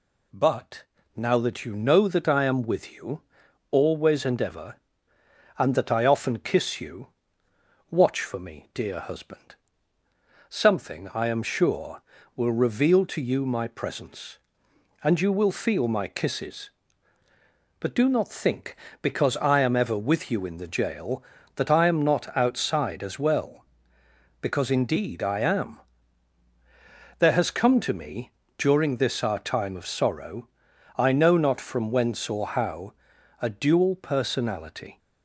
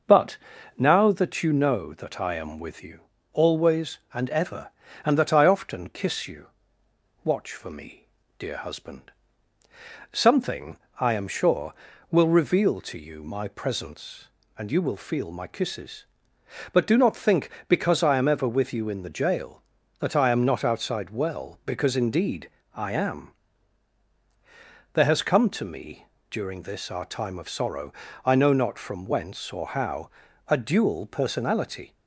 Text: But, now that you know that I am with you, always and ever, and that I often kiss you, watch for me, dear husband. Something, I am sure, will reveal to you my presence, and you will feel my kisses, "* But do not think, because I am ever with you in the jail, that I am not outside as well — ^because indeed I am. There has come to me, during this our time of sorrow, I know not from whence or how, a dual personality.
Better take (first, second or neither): first